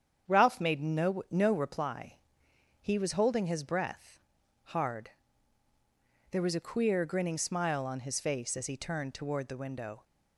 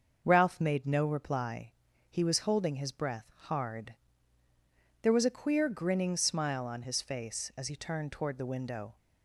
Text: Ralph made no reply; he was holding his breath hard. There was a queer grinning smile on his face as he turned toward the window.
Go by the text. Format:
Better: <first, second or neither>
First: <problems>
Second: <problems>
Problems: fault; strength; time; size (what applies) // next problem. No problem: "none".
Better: second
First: starts louder than the rest; strong; until 1.3 s; 8 dB // says "no" twice; at 1.2 s // pauses between "breath" and "hard"; noticeable; at 4.2 s; 0.46 s long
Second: starts louder than the rest; until 1.2 s; 6.5 dB